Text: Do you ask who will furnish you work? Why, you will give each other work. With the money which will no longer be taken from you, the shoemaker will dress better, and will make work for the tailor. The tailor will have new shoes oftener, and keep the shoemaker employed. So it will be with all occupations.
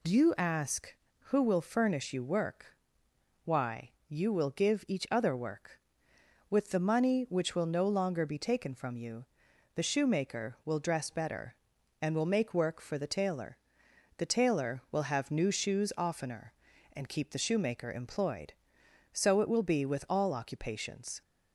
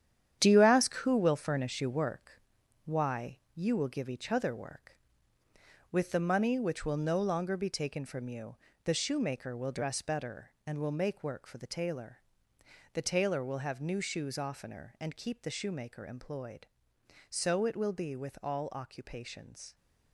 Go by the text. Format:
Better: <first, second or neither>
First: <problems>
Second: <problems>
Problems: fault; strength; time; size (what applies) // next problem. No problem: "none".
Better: first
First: none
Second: gets quieter; strong; throughout; 8.5 dB